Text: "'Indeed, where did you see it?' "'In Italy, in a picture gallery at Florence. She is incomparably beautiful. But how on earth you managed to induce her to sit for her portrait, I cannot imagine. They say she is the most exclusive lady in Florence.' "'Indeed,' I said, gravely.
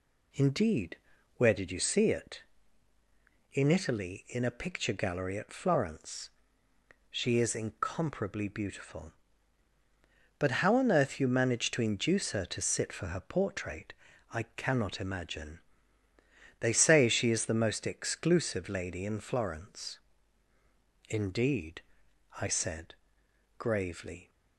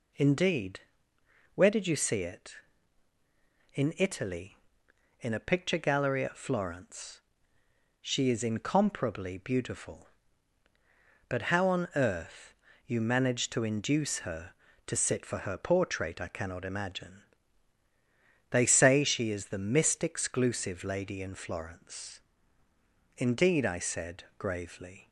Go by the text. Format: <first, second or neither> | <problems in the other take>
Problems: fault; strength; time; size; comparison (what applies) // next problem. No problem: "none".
first | pauses between "earth" and "you"; slight; at 12.5 s; 0.32 s long // says "mist" for "most"; at 19.5 s